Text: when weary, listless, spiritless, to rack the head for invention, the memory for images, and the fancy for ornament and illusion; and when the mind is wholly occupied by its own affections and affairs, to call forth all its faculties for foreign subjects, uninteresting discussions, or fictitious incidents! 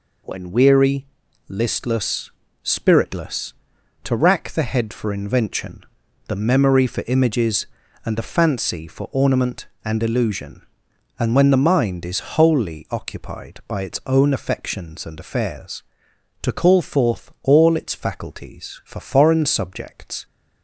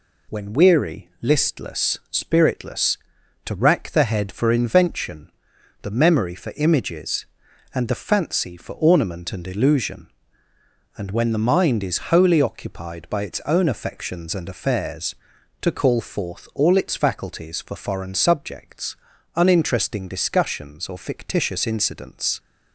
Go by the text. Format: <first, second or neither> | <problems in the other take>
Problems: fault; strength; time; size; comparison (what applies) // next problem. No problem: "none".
second | stops before "uninteresting discussions or fictitious incidents"; at 20.2 s